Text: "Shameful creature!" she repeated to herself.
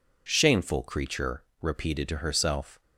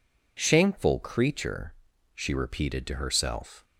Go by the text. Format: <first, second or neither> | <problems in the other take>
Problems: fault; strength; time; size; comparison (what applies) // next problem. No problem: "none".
second | skips "she"; at 1.5 s